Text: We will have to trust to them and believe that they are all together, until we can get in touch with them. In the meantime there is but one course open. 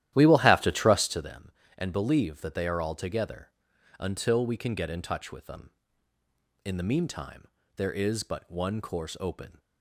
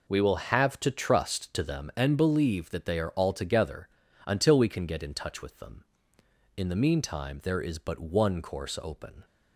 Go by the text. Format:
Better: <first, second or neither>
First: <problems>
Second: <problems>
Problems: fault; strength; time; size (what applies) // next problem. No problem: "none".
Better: second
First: starts louder than the rest; strong; until 1.3 s; 13 dB // pauses between "meantime" and "there"; slight; at 7.4 s; 0.30 s long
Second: none